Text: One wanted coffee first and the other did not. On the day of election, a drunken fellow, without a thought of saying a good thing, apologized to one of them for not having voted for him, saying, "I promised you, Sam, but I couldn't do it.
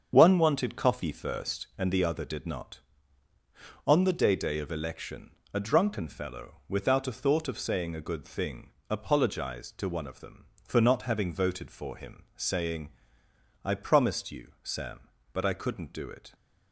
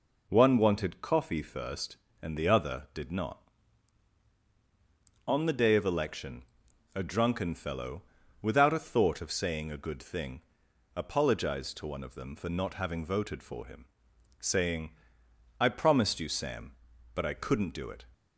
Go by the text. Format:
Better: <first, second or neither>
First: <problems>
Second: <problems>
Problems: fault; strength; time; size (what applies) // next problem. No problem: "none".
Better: second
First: starts louder than the rest; strong; until 1.1 s; 7.5 dB // says "day" twice; at 4.3 s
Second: none